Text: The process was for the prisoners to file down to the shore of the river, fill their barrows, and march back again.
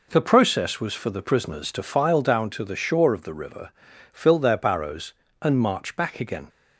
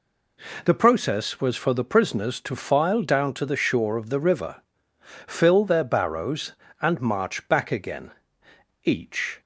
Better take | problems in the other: first | goes on to say "Each"; from 8.8 s on; 0.56 s long

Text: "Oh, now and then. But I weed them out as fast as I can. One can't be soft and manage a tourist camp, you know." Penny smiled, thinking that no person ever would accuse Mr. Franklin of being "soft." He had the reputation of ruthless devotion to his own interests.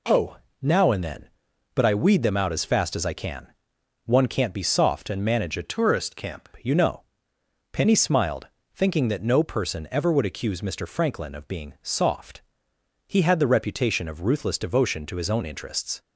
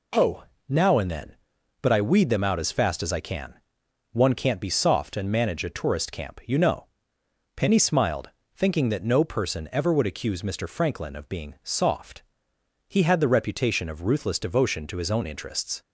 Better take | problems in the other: second | changes voice from "tourist" to "camp"; from 5.6 to 6.4 s; 0.8 s long

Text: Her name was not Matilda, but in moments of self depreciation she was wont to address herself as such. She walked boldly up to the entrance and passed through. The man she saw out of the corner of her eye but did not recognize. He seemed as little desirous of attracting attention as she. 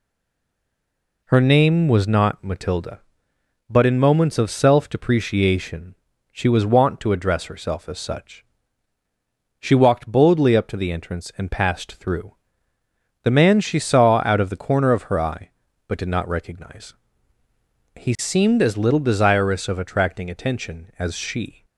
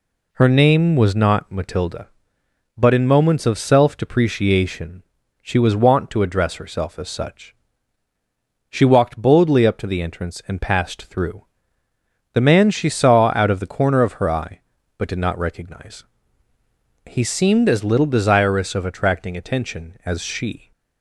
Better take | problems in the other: second | stays silent before the first word; noticeable; until 1.2 s; 1.2 s long // pauses between "depreciation" and "she"; slight; at 5.9 s; 0.36 s long; also in the second

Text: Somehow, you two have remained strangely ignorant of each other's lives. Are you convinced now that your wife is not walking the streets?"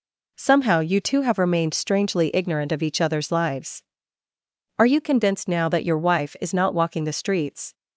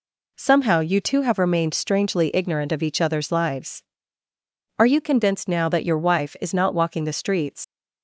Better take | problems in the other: first | leaves "streets" unfinished; at 7.6 s; 90 ms

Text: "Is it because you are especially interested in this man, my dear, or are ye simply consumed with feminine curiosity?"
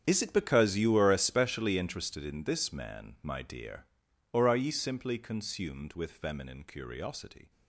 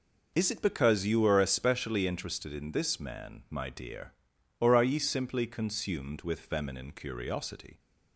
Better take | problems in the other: second | gets quieter; strong; throughout; 16 dB

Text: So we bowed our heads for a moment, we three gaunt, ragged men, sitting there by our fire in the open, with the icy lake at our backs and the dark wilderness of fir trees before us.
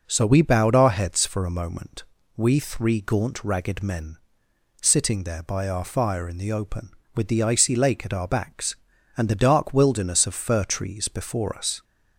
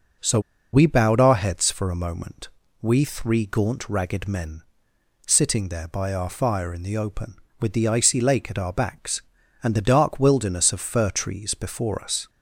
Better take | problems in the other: first | pauses between "So" and "we"; slight; at 0.4 s; 0.32 s long

